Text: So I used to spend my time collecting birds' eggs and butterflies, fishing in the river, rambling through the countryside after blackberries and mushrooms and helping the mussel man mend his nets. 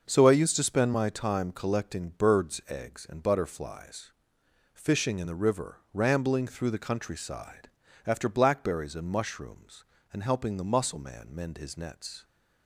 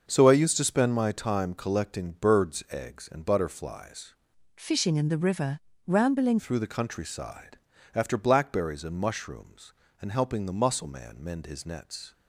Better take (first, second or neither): first